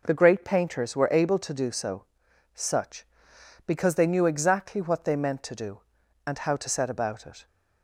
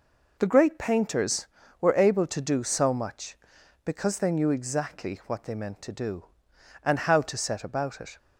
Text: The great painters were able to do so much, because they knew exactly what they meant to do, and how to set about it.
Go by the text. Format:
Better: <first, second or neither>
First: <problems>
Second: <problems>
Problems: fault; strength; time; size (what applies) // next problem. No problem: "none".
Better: second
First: says "such" for "much"; at 2.5 s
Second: none